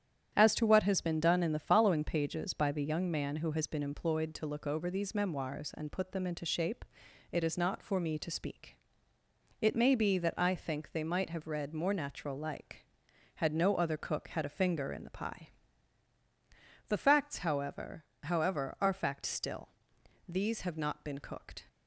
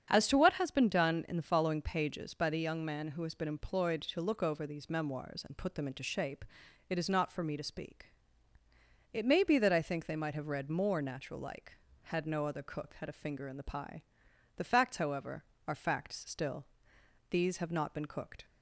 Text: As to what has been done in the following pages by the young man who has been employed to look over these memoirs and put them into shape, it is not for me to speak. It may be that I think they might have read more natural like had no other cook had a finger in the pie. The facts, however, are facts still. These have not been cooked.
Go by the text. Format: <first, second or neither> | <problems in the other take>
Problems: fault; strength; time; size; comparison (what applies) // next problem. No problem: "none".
second | starts louder than the rest; strong; until 1.3 s; 9.5 dB; strong in the second // says "however" twice; at 18.2 s